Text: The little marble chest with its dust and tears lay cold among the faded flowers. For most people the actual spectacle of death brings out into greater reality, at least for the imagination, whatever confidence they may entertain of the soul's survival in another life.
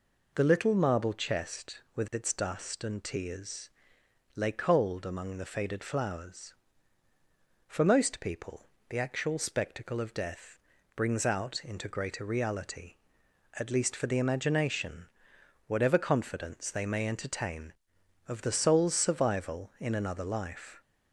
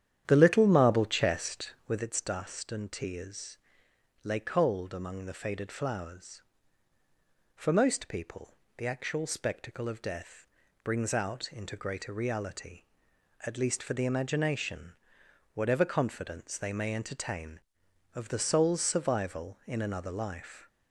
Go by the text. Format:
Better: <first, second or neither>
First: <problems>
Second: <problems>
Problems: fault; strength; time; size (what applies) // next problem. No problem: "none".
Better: first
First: pauses between "tears" and "lay"; noticeable; at 3.7 s; 0.64 s long // pauses between "people" and "the"; slight; at 8.6 s; 0.20 s long // pauses between "death" and "brings"; slight; at 10.5 s; 0.36 s long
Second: starts louder than the rest; strong; until 2.1 s; 10 dB // pauses between "tears" and "lay"; noticeable; at 3.5 s; 0.64 s long // pauses between "people" and "the"; slight; at 8.5 s; 0.20 s long // pauses between "death" and "brings"; slight; at 10.4 s; 0.36 s long